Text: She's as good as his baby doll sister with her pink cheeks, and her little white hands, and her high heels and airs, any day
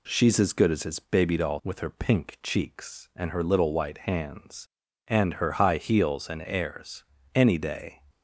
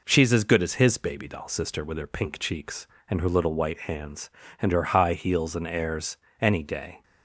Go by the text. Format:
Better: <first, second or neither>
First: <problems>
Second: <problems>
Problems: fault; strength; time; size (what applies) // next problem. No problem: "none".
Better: second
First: skips "sister"; at 1.5 s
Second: none